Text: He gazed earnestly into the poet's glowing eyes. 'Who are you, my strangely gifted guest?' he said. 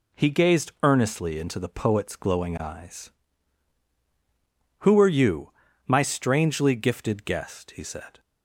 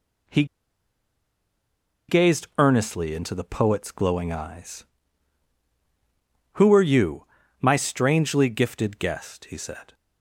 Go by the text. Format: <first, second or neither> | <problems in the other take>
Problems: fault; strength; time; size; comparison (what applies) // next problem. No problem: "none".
first | pauses between "He" and "gazed"; strong; at 0.4 s; 1.6 s long